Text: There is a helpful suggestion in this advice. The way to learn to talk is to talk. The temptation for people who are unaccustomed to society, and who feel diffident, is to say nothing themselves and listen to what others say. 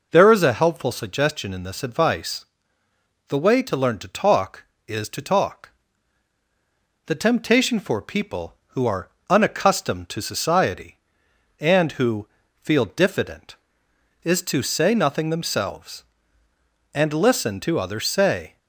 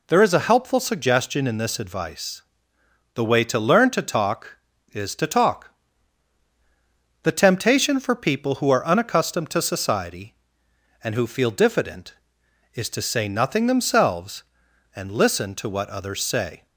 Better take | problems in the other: second | pauses between "are" and "unaccustomed"; slight; at 9.0 s; 0.20 s long // pauses between "who" and "feel"; slight; at 12.2 s; 0.34 s long // skips "what"; at 17.7 s

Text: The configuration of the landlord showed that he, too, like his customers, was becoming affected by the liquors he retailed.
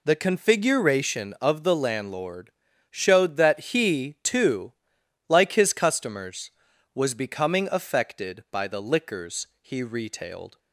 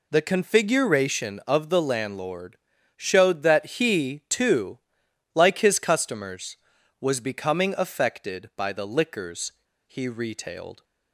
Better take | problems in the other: first | pauses between "landlord" and "showed"; at 2.5 s; 0.38 s long; also in the first // pauses between "liquors" and "he"; slight; at 9.5 s; 0.34 s long

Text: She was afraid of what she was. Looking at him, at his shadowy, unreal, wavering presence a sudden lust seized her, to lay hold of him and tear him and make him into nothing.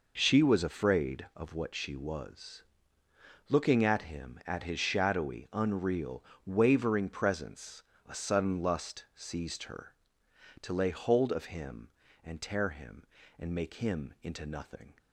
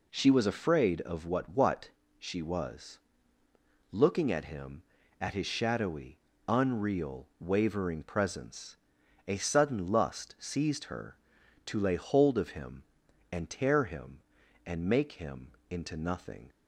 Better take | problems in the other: first | says "what" twice; at 1.4 s // pauses between "presence" and "a"; noticeable; at 8.7 s; 0.52 s long; slight in the first // pauses between "him" and "into"; slight; at 15.5 s; 0.18 s long

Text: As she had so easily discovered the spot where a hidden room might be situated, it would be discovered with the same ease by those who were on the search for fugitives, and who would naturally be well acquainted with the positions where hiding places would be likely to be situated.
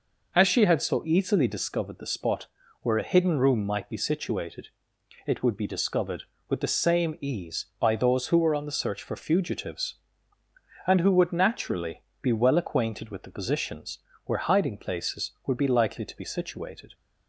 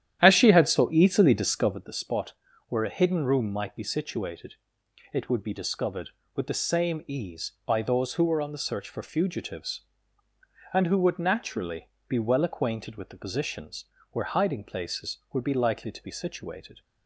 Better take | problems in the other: first | starts louder than the rest; strong; until 1.8 s; 11 dB // pauses between "spot" and "where"; slight; at 2.3 s; 0.36 s long; slight in the first // pauses between "naturally" and "be"; slight; at 11.8 s; 0.20 s long; slight in the first // pauses between "positions" and "where"; slight; at 13.8 s; 0.28 s long; slight in the first

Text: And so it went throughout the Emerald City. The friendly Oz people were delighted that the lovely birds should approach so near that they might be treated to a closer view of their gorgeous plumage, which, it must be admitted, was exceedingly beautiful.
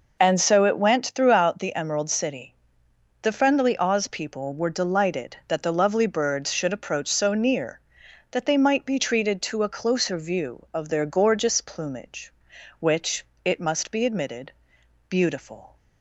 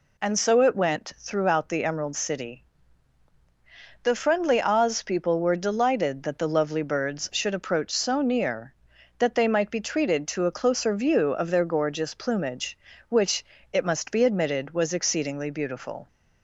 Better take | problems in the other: second | skips "was exceedingly"; at 14.7 s

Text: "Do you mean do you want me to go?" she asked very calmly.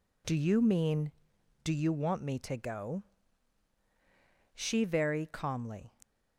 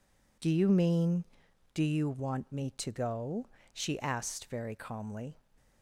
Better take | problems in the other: second | skips "asked"; at 4.8 s

